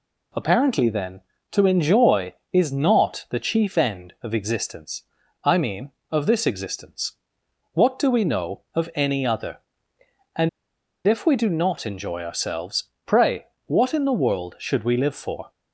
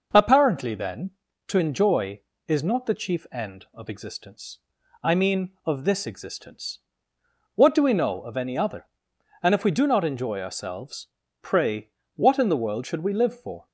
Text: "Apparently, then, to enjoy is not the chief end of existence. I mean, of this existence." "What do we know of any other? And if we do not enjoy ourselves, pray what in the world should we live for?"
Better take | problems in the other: second | pauses between "And" and "if"; noticeable; at 10.4 s; 0.57 s long // pauses between "pray" and "what"; slight; at 13.4 s; 0.22 s long; slight in the second

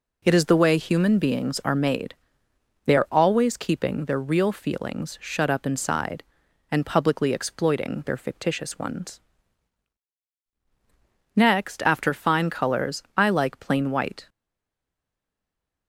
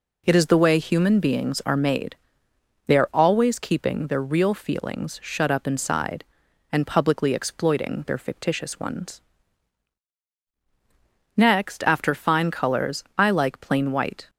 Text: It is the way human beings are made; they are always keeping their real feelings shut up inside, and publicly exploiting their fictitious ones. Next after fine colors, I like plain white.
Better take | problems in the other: second | stays silent after the last word; noticeable; from 14.2 s on; 1.6 s long

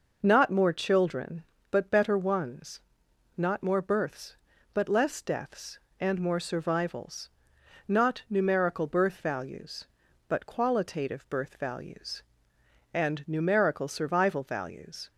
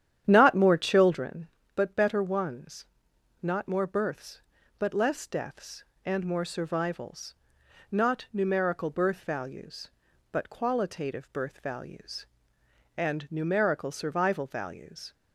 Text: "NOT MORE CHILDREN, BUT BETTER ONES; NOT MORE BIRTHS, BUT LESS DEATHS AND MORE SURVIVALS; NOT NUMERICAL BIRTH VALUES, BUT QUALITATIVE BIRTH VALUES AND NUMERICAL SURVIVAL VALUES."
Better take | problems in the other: first | starts louder than the rest; strong; until 1.3 s; 10 dB

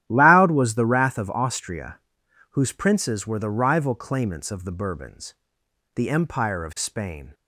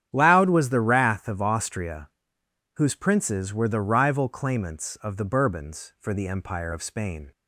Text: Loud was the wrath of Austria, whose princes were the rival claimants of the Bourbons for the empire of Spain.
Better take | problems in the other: second | starts louder than the rest; strong; until 1.0 s; 11.5 dB; strong in the second // skips "for"; at 5.6 s

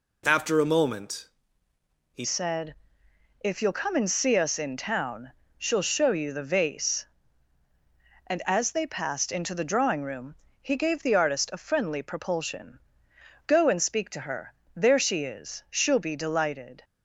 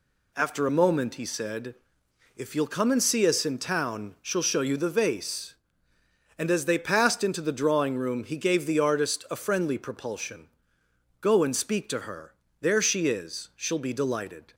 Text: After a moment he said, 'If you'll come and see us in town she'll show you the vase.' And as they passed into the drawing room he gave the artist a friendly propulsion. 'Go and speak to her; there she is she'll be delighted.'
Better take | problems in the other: second | pauses between "moment" and "he"; noticeable; at 1.2 s; 0.88 s long // changes voice at "said"; from 2.2 s on; 14.6 s long // pauses between "town" and "she'll"; slight; at 5.3 s; 0.26 s long // pauses between "room" and "he"; slight; at 10.3 s; 0.24 s long

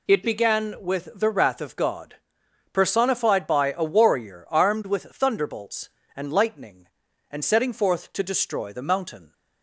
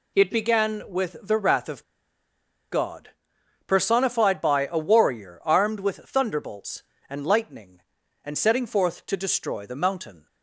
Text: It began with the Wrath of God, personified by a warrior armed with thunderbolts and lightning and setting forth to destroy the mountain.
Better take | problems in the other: first | pauses between "of" and "God"; noticeable; at 1.8 s; 0.88 s long

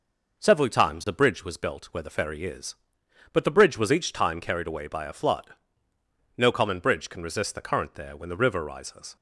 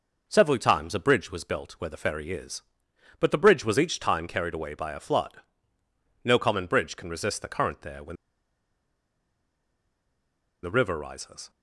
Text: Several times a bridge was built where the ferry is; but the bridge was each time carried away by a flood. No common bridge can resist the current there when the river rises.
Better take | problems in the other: first | pauses between "when" and "the"; strong; at 8.1 s; 2.4 s long

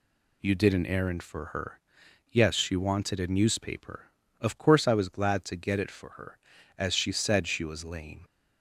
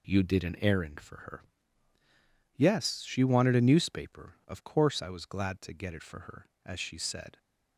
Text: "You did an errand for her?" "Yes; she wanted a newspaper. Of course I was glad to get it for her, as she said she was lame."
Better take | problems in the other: first | stops before "she was lame"; at 7.3 s

